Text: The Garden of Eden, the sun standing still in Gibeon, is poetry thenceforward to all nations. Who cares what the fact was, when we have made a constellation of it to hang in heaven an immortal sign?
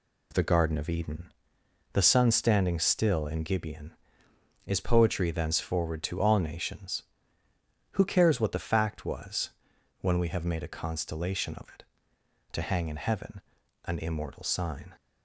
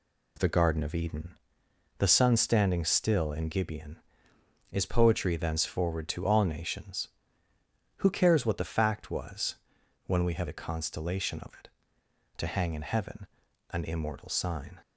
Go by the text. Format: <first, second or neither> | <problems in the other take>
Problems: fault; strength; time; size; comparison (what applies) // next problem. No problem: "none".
first | skips "made"; at 10.4 s // pauses between "heaven" and "an"; at 13.2 s; 0.42 s long; also in the first